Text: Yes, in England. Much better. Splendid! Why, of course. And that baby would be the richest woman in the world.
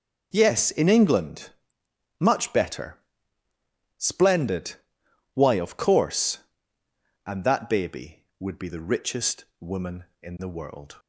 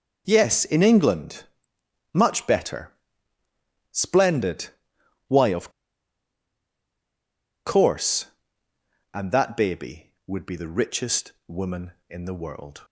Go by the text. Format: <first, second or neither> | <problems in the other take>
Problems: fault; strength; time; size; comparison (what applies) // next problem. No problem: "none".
first | starts louder than the rest; noticeable; until 1.2 s; 6 dB; noticeable in the first // pauses between "of" and "course"; strong; at 5.6 s; 1.9 s long // pauses between "richest" and "woman"; slight; at 11.3 s; 0.16 s long; slight in the first